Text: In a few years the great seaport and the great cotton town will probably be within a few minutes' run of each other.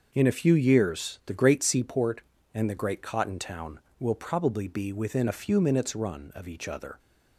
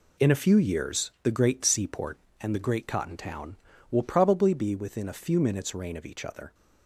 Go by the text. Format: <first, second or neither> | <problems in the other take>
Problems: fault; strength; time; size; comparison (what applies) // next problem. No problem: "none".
first | says "rain" for "run"; at 5.7 s